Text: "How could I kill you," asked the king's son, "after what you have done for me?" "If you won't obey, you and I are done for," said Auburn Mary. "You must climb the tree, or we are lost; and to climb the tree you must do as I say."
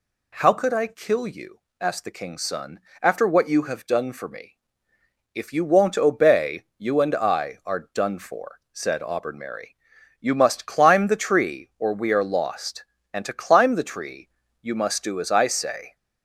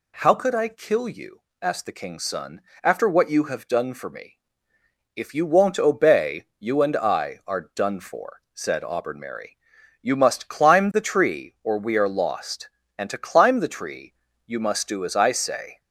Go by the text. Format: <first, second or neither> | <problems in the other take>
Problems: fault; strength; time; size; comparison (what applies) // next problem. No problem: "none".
neither | pauses between "tree" and "you"; slight; the same in both